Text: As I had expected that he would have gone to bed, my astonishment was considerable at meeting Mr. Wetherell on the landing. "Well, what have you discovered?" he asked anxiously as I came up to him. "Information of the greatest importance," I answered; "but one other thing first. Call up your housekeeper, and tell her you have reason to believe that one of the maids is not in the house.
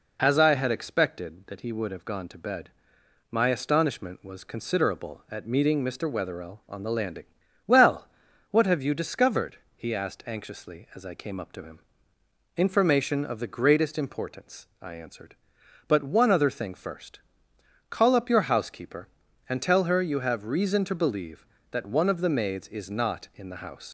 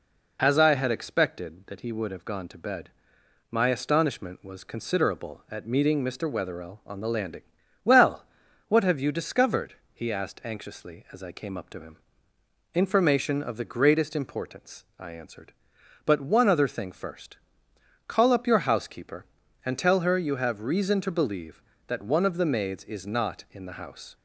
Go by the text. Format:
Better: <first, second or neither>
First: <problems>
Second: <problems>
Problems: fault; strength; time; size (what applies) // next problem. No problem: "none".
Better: second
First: leaves "house" unfinished; at 23.8 s; 60 ms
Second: none